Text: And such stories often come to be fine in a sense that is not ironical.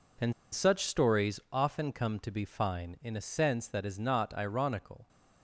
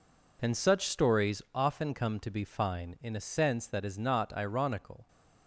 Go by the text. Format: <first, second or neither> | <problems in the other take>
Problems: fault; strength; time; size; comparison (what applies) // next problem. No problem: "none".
second | pauses between "And" and "such"; slight; at 0.3 s; 0.21 s long